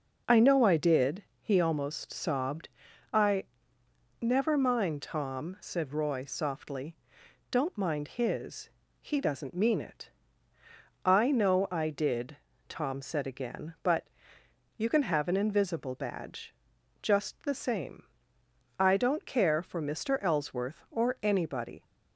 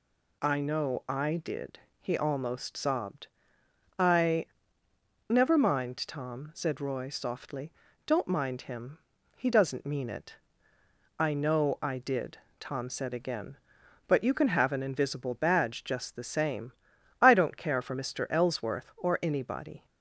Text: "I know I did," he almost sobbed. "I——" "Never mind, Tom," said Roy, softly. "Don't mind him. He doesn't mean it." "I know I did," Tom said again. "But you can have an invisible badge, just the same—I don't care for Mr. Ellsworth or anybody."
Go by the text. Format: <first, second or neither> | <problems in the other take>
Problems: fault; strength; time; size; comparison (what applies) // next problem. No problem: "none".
second | says "his" for "him"; at 8.0 s // pauses between "But" and "you"; noticeable; at 14.0 s; 0.68 s long